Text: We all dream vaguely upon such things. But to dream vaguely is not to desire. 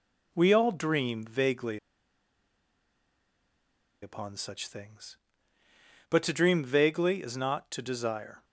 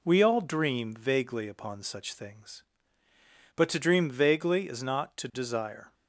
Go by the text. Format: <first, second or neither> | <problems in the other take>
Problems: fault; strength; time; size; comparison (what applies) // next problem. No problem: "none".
second | pauses between "vaguely" and "upon"; strong; at 1.7 s; 2.2 s long